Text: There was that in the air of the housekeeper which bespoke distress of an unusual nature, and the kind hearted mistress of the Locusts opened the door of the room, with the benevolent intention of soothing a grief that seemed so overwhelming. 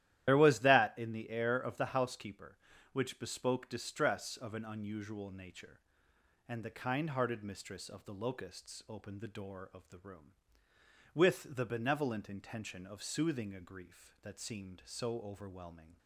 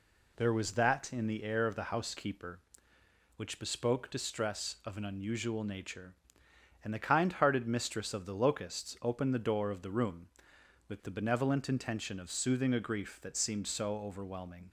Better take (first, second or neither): second